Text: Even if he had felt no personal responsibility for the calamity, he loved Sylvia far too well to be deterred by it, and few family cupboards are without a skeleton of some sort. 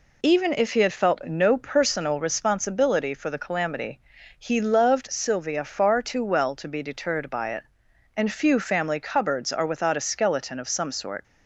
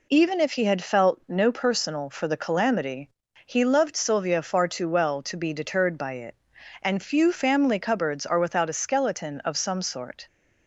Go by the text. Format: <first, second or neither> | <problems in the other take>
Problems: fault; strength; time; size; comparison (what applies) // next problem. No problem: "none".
first | skips "responsibility"; at 2.0 s